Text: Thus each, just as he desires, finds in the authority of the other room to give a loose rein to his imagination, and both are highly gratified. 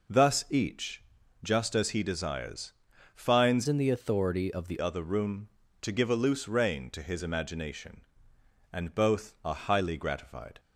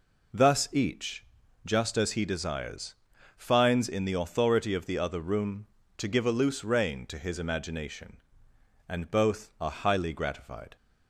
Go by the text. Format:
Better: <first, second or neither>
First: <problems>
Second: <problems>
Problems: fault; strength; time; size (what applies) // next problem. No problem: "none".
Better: second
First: changes voice from "in" to "the"; from 3.6 to 4.7 s; 1.1 s long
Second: none